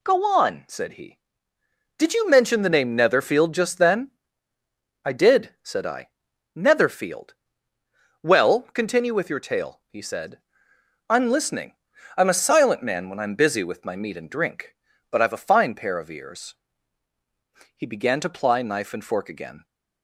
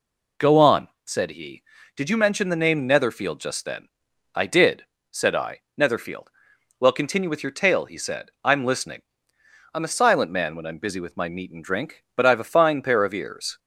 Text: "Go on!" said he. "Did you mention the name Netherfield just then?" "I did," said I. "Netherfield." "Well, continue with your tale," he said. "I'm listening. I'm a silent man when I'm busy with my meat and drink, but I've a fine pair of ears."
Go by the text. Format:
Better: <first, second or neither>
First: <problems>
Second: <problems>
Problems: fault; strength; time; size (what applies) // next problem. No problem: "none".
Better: second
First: goes on to say "He began to ply knife and fork again"; strong; from 17.7 s on; 1.8 s long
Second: none